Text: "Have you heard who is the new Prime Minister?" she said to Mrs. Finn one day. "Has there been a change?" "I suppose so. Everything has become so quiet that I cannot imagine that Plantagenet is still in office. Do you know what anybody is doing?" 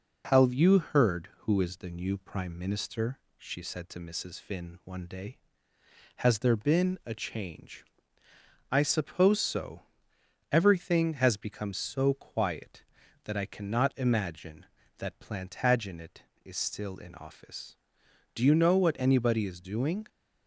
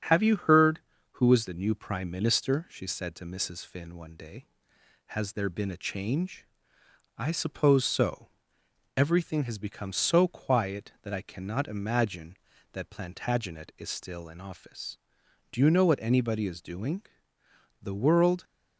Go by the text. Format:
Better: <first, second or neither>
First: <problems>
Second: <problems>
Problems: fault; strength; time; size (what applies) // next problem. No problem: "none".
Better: first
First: none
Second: starts louder than the rest; strong; until 1.3 s; 8 dB // goes on to say "The world"; noticeable; from 17.8 s on; 0.62 s long